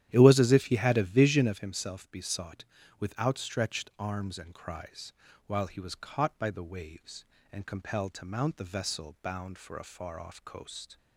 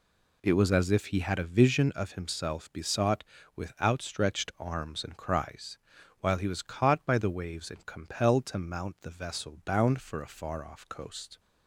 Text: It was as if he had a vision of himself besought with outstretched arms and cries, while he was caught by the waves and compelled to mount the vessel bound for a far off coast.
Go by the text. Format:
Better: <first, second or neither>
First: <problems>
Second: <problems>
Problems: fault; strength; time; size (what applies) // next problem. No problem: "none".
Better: second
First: starts louder than the rest; strong; until 1.7 s; 11.5 dB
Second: none